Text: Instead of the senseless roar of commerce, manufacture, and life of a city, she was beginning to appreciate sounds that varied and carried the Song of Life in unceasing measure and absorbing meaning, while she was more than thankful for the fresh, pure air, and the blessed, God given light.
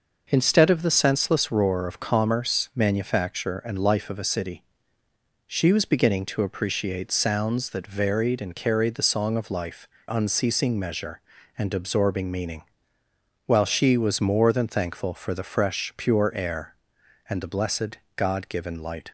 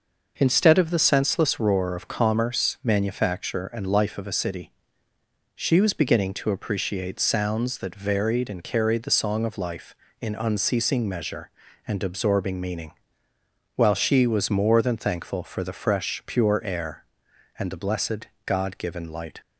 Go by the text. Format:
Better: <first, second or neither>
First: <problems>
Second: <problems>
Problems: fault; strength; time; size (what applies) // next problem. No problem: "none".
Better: second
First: skips "in"; at 9.9 s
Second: none